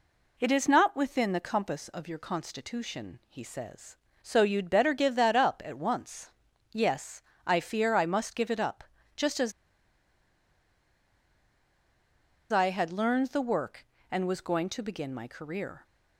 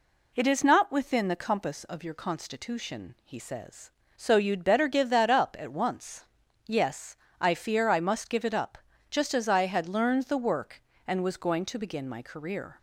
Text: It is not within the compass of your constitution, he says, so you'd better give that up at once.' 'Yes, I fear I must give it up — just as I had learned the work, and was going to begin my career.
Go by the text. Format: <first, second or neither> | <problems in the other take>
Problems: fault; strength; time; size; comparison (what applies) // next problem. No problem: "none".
second | pauses between "as" and "I"; strong; at 9.5 s; 3.0 s long